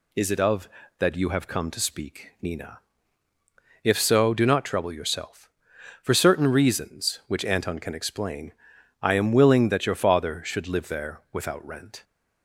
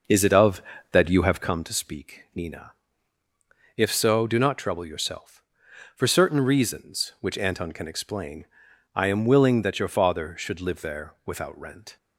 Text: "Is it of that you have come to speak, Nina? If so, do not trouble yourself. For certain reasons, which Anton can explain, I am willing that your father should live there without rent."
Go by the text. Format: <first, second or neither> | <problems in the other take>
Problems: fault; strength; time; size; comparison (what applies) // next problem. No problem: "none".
first | starts louder than the rest; noticeable; until 1.7 s; 6 dB